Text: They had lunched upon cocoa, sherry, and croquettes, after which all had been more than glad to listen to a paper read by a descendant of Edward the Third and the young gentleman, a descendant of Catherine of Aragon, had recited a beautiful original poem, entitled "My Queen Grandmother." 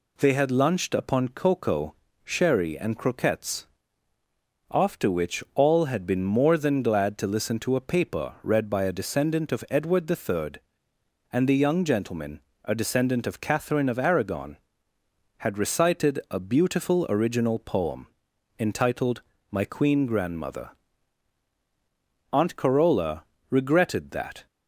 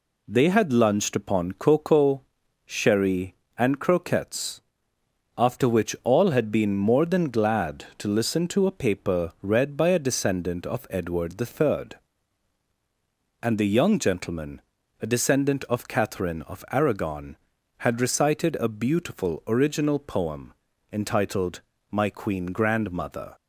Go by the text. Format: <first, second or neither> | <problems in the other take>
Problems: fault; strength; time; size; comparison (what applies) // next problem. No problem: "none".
second | pauses between "entitled" and "My"; slight; at 19.2 s; 0.30 s long; slight in the second // goes on to say "Aunt Carola regretted that"; strong; from 22.3 s on; 2.1 s long